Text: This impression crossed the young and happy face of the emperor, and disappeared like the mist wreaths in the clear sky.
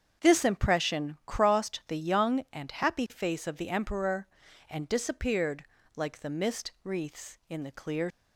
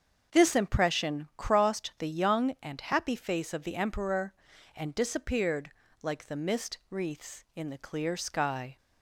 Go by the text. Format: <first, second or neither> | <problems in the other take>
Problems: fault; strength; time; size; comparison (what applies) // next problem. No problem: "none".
second | starts louder than the rest; strong; until 1.3 s; 7.5 dB; also in the second // pauses between "disappeared" and "like"; slight; at 5.6 s; 0.32 s long; slight in the second // stops before "sky"; at 8.1 s